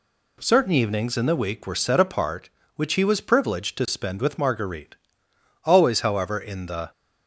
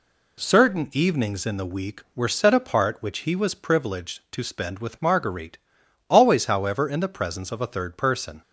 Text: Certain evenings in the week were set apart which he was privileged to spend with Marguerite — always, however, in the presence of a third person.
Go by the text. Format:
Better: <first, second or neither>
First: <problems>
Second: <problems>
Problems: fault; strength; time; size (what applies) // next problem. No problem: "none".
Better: second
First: stops before "presence of a third person"; at 6.9 s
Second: none